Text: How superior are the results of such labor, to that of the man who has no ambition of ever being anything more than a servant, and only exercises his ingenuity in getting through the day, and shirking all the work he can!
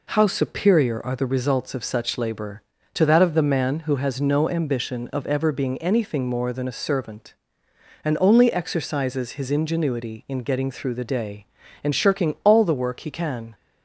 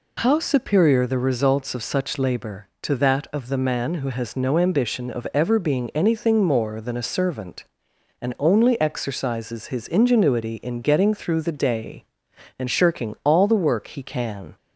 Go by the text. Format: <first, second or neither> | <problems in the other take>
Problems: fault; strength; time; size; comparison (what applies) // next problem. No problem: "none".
first | skips "are"; at 1.0 s